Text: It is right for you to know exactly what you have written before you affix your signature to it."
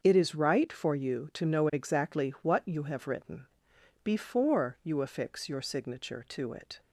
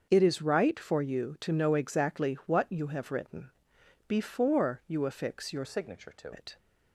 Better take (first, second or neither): first